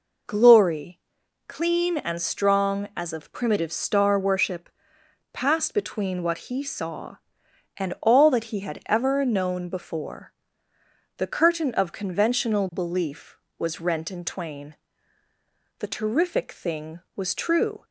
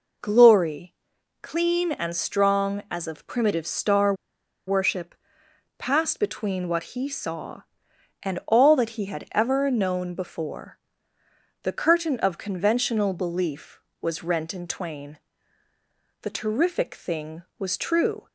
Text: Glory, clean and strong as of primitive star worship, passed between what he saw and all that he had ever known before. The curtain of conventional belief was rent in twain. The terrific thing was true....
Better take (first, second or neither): first